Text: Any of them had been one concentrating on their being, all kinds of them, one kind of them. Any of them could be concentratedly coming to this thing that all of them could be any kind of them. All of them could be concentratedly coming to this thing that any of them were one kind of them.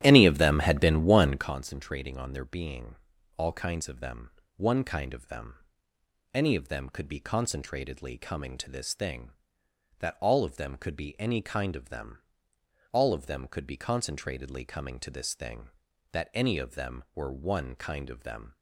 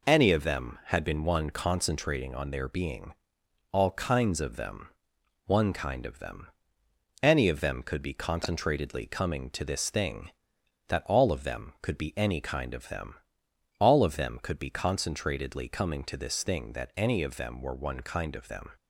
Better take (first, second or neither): second